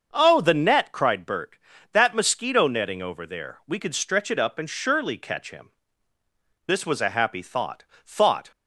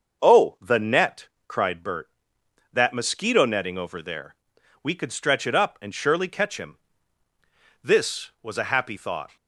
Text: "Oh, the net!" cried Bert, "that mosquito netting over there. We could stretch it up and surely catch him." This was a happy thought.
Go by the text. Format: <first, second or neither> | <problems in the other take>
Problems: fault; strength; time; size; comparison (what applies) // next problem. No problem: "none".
second | starts louder than the rest; until 1.1 s; 6.5 dB; also in the second // says "thought" twice; at 8.0 s